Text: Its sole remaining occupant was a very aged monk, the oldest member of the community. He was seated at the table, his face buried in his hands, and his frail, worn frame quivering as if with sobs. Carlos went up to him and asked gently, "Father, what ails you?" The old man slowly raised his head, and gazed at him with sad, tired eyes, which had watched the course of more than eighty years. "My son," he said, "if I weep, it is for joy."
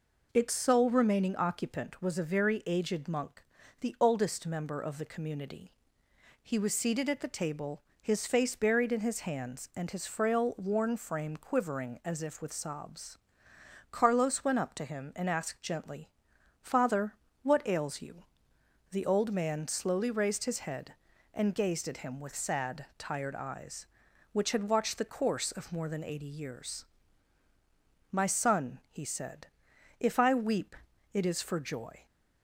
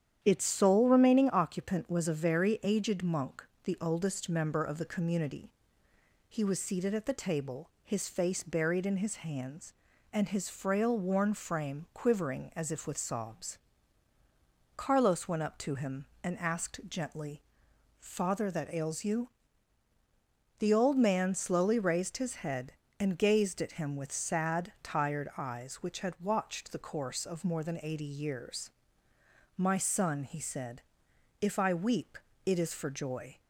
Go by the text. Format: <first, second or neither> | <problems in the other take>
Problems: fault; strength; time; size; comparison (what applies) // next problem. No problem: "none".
first | starts louder than the rest; strong; until 1.2 s; 9.5 dB // says "that" for "what"; at 18.5 s